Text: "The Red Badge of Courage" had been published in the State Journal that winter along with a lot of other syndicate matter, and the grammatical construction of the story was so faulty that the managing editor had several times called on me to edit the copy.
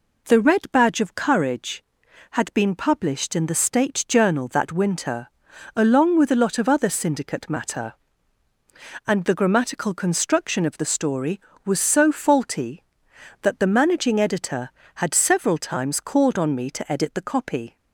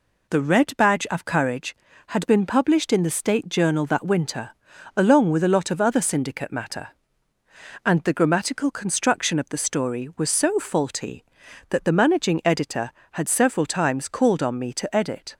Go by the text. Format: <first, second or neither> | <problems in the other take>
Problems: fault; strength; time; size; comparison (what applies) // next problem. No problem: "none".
first | pauses between "winter" and "along"; noticeable; at 4.5 s; 0.46 s long; noticeable in the first // stops before "the copy"; at 15.3 s